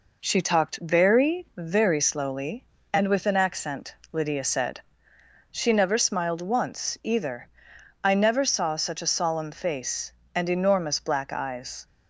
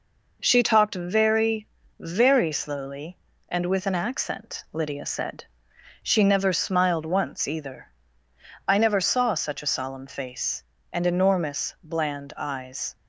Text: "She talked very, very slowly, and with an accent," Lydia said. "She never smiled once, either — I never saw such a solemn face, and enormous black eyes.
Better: first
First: none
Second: says "bland" for "black"; at 11.8 s

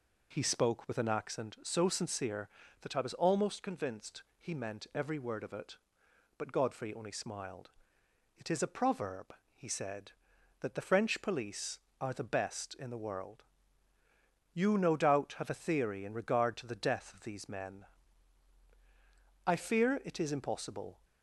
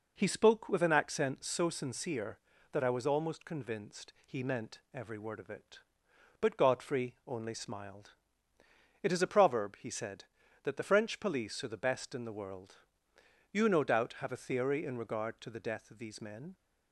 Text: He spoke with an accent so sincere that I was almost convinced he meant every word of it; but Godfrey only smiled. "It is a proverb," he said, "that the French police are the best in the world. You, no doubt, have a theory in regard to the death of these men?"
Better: second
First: pauses between "convinced" and "he"; slight; at 4.2 s; 0.16 s long // goes on to say "I fear it is impossible"; from 19.4 s on; 1.5 s long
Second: none

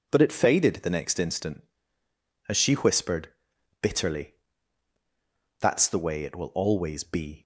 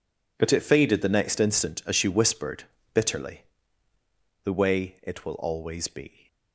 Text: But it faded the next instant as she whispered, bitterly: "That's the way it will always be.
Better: first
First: none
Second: skips "That's"; at 3.9 s

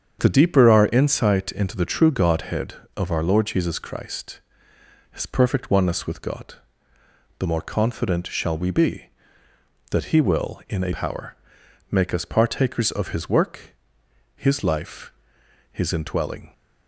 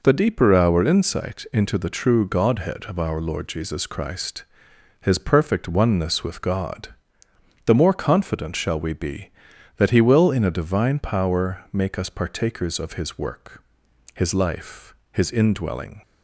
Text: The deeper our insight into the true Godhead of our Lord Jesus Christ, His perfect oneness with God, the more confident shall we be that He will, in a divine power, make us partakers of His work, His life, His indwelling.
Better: second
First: starts louder than the rest; strong; until 1.2 s; 7.5 dB // skips "divine"; at 10.9 s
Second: none

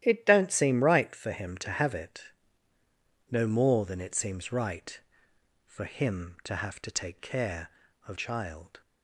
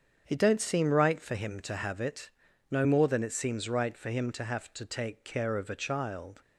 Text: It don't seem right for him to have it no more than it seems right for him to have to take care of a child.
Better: second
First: starts louder than the rest; strong; until 1.0 s; 12 dB // pauses between "it" and "no"; at 2.2 s; 1.0 s long // skips "a"; at 8.1 s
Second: starts louder than the rest; strong; until 1.2 s; 7.5 dB // pauses between "it" and "no"; at 2.2 s; 0.42 s long

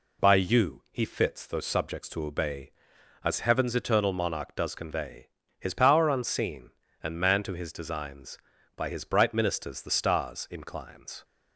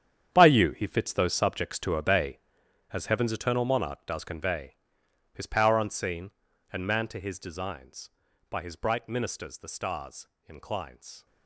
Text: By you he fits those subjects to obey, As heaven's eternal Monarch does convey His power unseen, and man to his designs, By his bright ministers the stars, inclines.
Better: first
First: pauses between "convey" and "His"; slight; at 5.2 s; 0.30 s long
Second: gets quieter; strong; throughout; 14.5 dB // pauses between "convey" and "His"; noticeable; at 4.7 s; 0.58 s long

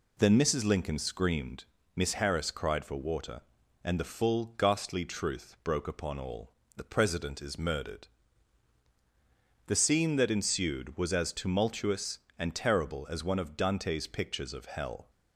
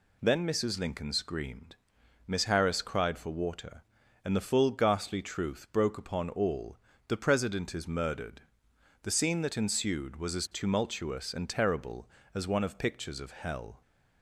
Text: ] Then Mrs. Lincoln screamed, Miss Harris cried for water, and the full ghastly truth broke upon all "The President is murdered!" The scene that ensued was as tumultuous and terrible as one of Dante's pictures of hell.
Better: first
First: pauses between "all" and "The"; slight; at 6.5 s; 0.24 s long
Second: pauses between "all" and "The"; slight; at 6.7 s; 0.30 s long // skips "Dante's"; at 12.7 s

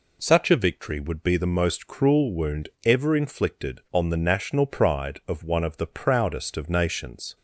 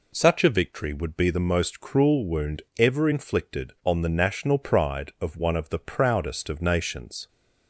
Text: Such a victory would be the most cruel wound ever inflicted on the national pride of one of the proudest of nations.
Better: neither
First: pauses between "wound" and "ever"; slight; at 2.6 s; 0.16 s long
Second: pauses between "wound" and "ever"; slight; at 2.6 s; 0.16 s long

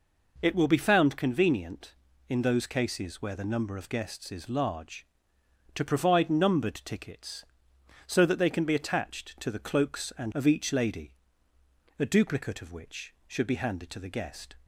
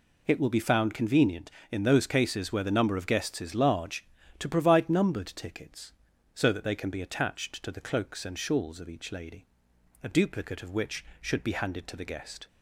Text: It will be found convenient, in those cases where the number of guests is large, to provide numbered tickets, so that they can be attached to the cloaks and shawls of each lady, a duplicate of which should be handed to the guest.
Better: second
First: skips "shawls"; at 10.3 s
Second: none

